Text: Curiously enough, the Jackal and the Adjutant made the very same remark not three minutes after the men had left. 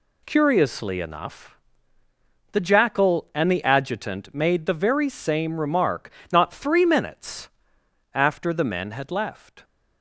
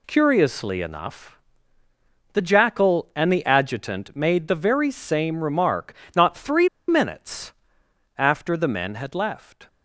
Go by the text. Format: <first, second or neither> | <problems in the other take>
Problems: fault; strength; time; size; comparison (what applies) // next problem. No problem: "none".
first | pauses between "remark" and "not"; slight; at 5.9 s; 0.20 s long; slight in the first // pauses between "three" and "minutes"; slight; at 6.6 s; 0.20 s long // pauses between "minutes" and "after"; noticeable; at 7.5 s; 0.64 s long; noticeable in the first